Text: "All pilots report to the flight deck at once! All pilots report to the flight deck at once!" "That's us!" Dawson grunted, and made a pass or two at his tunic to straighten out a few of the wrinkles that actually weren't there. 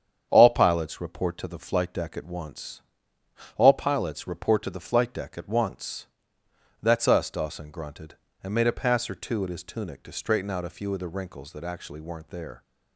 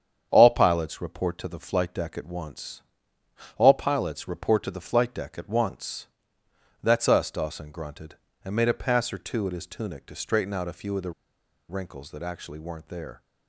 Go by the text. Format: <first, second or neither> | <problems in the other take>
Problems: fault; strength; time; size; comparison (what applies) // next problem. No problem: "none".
first | starts louder than the rest; strong; until 1.3 s; 8 dB; strong in the first // pauses between "the" and "wrinkles"; noticeable; at 11.1 s; 0.57 s long